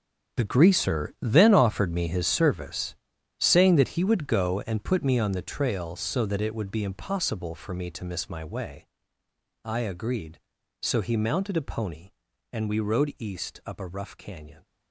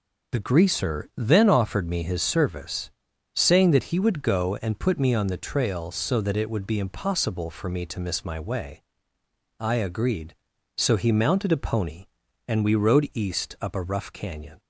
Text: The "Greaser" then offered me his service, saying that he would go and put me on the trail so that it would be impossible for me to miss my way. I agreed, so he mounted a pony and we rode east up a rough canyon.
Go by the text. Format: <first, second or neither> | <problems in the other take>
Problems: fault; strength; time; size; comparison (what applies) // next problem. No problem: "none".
second | gets quieter; strong; throughout; 13 dB